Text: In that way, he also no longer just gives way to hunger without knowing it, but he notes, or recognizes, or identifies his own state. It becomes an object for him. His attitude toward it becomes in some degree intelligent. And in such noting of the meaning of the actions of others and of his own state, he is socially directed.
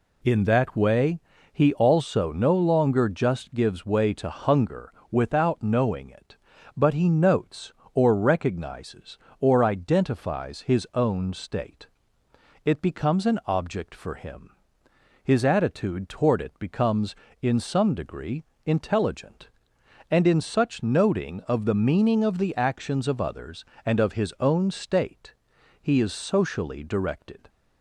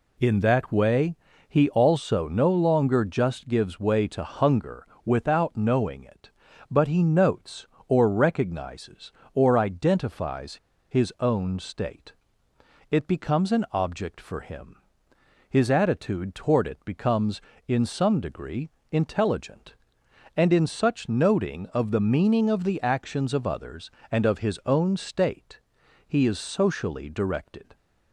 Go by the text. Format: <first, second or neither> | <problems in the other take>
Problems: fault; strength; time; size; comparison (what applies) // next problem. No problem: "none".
first | pauses between "hunger" and "without"; slight; at 4.8 s; 0.20 s long; slight in the first // pauses between "identifies" and "his"; slight; at 10.5 s; 0.34 s long // pauses between "degree" and "intelligent"; slight; at 18.6 s; 0.22 s long; slight in the first